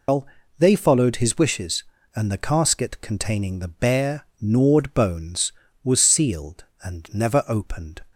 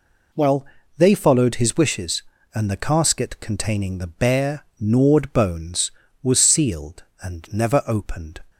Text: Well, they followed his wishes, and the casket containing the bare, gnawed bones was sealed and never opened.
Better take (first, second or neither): second